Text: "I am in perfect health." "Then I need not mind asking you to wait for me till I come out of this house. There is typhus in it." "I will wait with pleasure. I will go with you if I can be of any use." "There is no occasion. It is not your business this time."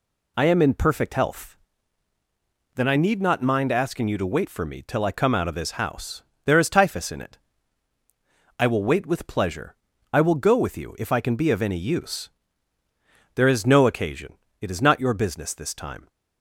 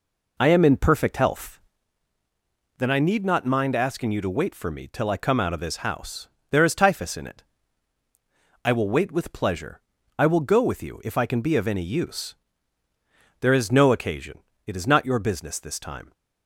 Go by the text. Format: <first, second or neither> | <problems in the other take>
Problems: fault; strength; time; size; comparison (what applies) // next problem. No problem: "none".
first | starts louder than the rest; until 1.8 s; 4 dB